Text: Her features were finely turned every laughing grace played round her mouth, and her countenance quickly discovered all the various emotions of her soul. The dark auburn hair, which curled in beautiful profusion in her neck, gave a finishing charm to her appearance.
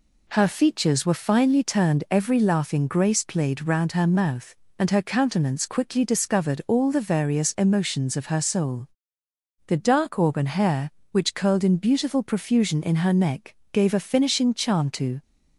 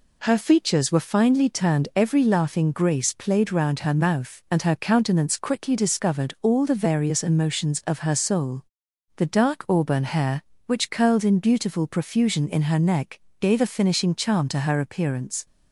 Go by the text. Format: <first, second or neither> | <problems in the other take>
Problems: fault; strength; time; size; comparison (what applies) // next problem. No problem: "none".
second | stops before "her appearance"; at 15.2 s